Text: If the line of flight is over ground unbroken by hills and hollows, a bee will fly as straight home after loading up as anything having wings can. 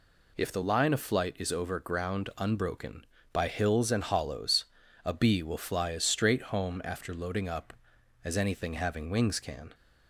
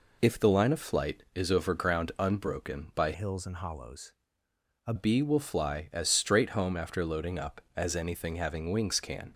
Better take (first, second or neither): first